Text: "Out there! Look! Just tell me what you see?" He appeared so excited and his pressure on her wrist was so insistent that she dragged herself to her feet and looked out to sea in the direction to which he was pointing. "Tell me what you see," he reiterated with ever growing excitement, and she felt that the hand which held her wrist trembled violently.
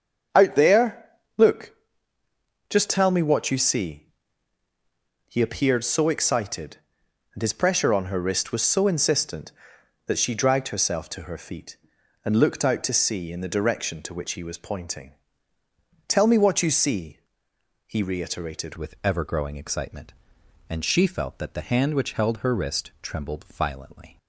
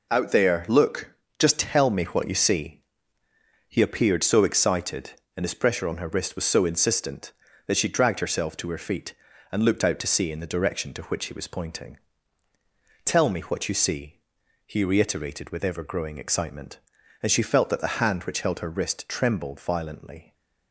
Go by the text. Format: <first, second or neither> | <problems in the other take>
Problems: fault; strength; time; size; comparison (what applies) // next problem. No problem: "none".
second | starts louder than the rest; strong; until 1.5 s; 7.5 dB // changes voice at "with"; from 18.7 s on; 5.4 s long